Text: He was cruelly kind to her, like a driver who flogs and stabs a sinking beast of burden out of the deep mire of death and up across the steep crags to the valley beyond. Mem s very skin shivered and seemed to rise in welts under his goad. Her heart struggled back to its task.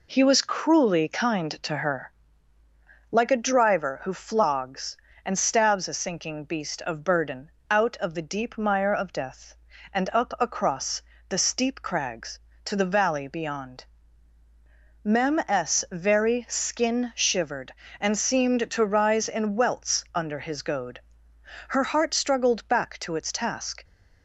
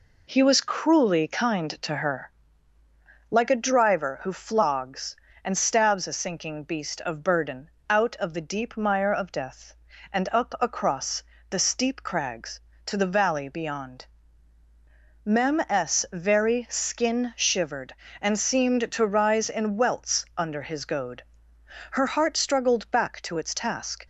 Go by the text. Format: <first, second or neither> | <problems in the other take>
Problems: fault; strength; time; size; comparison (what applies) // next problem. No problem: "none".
neither | pauses between "burden" and "out"; slight; the same in both // pauses between "across" and "the"; slight; the same in both